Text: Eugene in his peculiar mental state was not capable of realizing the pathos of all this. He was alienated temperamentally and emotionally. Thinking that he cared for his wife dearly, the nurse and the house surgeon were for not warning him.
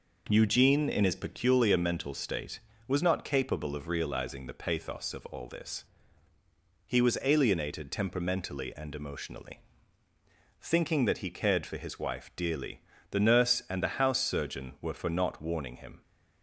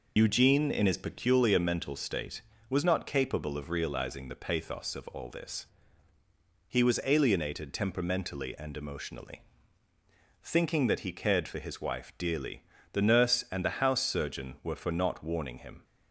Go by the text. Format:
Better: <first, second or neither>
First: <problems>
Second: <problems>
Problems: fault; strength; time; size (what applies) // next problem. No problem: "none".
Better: first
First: none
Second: loses the start of "Eugene"; at 0.1 s; 80 ms